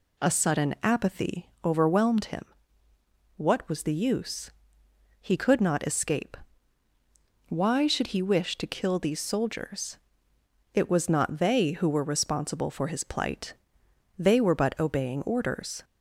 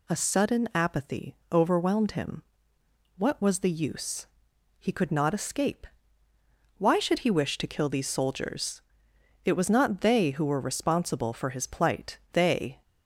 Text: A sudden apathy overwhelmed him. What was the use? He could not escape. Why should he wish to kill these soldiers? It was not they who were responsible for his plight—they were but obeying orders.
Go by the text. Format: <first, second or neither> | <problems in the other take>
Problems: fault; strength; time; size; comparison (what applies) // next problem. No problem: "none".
first | pauses between "apathy" and "overwhelmed"; slight; at 1.3 s; 0.16 s long; slight in the first // stops before "were but obeying orders"; at 12.8 s